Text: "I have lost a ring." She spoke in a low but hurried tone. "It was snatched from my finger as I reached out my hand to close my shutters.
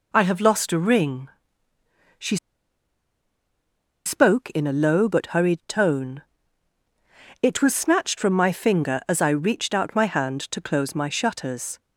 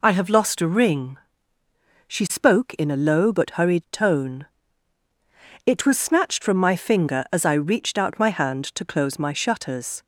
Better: second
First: pauses between "She" and "spoke"; strong; at 2.3 s; 1.6 s long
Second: none

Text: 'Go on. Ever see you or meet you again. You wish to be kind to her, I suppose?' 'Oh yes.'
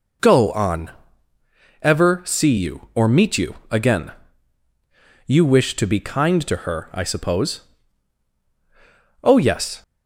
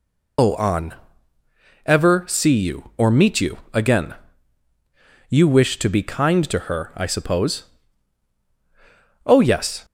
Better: first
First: pauses between "you" and "again"; slight; at 3.5 s; 0.16 s long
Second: loses the start of "Go"; at 0.3 s; 140 ms // pauses between "you" and "again"; slight; at 3.5 s; 0.16 s long

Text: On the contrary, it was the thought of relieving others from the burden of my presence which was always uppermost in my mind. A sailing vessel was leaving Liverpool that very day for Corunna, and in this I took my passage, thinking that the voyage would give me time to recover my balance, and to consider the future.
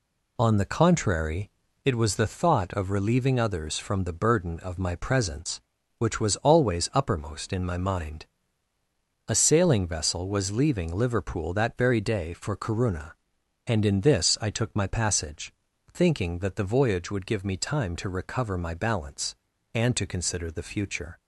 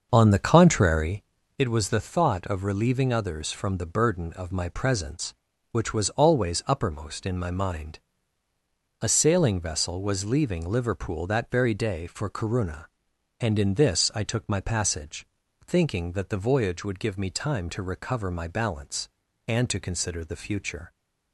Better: first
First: none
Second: starts louder than the rest; until 1.2 s; 6.5 dB

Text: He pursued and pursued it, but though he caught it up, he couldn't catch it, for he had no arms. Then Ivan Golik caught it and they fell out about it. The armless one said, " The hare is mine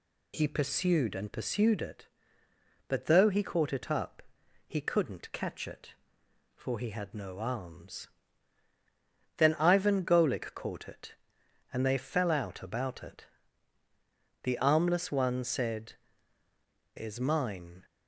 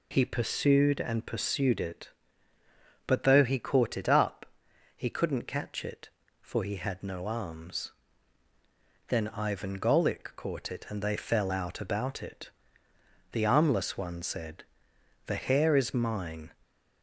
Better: second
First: skips "The hare"; at 16.9 s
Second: none

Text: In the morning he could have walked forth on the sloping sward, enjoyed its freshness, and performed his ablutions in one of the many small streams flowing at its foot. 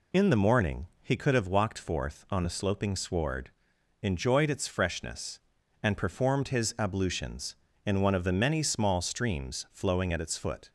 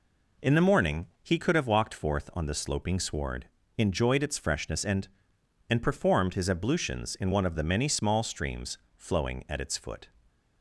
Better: first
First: none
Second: pauses between "morning" and "he"; slight; at 1.0 s; 0.16 s long // says "and" twice; at 5.6 s // pauses between "streams" and "flowing"; slight; at 8.7 s; 0.22 s long

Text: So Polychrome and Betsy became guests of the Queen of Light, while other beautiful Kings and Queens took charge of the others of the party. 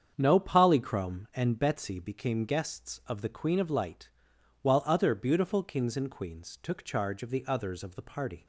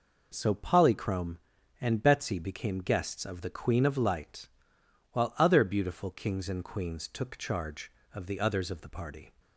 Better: second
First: starts louder than the rest; strong; until 1.1 s; 7.5 dB // says "No" for "So"; at 0.1 s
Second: none

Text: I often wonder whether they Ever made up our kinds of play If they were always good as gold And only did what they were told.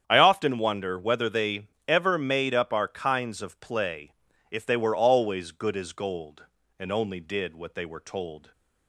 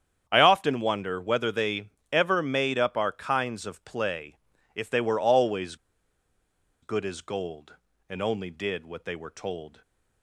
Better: first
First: starts louder than the rest; strong; until 1.0 s; 8.5 dB // pauses between "they" and "Ever"; slight; at 1.6 s; 0.22 s long // pauses between "play" and "If"; at 4.1 s; 0.38 s long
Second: starts louder than the rest; strong; until 1.2 s; 8.5 dB // pauses between "they" and "Ever"; slight; at 1.8 s; 0.24 s long // pauses between "play" and "If"; at 4.3 s; 0.38 s long // pauses between "always" and "good"; at 5.7 s; 1.0 s long

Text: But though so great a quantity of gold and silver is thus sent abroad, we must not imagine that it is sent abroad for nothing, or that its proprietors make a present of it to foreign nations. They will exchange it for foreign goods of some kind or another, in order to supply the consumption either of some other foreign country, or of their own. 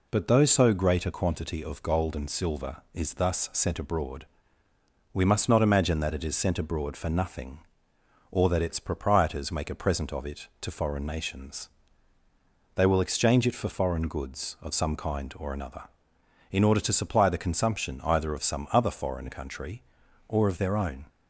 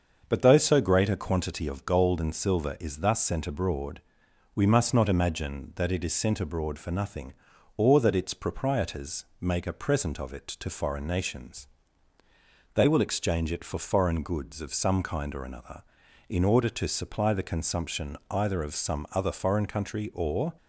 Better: first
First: none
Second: starts louder than the rest; until 1.2 s; 6.5 dB // pauses between "proprietors" and "make"; slight; at 9.2 s; 0.16 s long // stops before "of their own"; at 20.5 s

